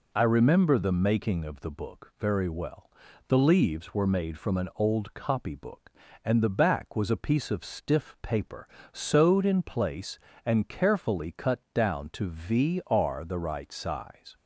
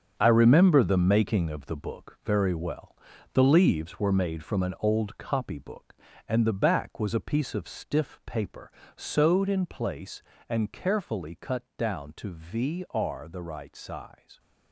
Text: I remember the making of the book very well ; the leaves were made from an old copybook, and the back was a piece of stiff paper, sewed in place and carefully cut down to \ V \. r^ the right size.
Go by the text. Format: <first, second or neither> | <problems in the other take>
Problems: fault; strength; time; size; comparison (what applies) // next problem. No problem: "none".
first | gets quieter; strong; throughout; 8.5 dB // pauses between "cut" and "down"; slight; at 11.6 s; 0.16 s long; slight in the first